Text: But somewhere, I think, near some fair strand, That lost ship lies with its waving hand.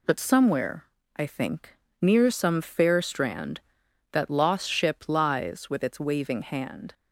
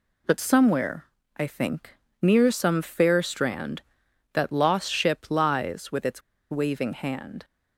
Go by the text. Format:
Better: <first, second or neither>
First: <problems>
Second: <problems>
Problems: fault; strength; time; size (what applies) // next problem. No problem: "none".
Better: first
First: none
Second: pauses between "its" and "waving"; slight; at 6.2 s; 0.29 s long